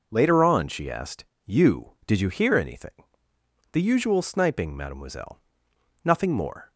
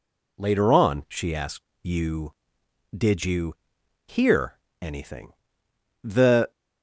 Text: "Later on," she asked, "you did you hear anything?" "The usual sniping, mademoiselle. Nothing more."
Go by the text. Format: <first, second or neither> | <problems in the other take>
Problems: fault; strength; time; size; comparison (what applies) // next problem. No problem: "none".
first | pauses between "you" and "hear"; noticeable; at 3.5 s; 0.52 s long // pauses between "hear" and "anything"; slight; at 4.5 s; 0.22 s long // stops before "usual sniping mademoiselle Nothing more"; at 6.5 s